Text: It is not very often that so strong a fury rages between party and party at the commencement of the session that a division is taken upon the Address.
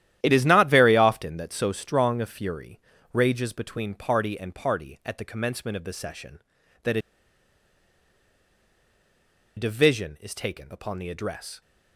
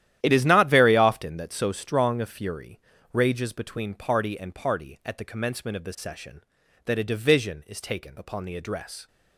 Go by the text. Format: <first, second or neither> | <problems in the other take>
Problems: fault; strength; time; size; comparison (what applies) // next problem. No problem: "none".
second | starts louder than the rest; strong; until 1.2 s; 12 dB; strong in the second // pauses between "fury" and "rages"; slight; at 2.7 s; 0.32 s long; slight in the second // pauses between "a" and "division"; strong; at 7.0 s; 2.5 s long